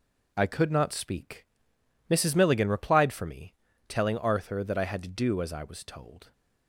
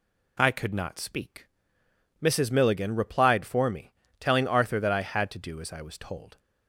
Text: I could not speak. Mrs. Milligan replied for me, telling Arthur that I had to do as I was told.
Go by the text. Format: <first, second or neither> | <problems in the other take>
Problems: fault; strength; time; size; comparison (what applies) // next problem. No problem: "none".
second | gets quieter; strong; throughout; 7.5 dB